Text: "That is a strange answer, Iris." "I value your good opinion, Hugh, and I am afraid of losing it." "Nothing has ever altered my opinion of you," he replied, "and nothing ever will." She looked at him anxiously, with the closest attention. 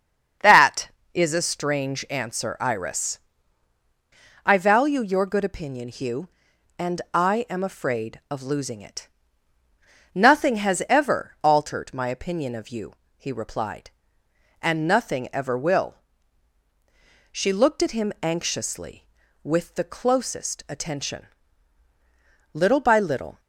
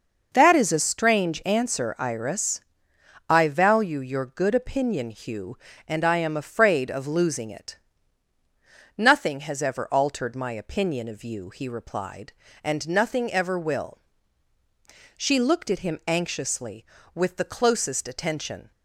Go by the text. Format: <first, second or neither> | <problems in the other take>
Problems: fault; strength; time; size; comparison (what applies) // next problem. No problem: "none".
second | starts louder than the rest; strong; until 1.6 s; 7 dB // goes on to say "Little by little"; noticeable; from 22.5 s on; 0.86 s long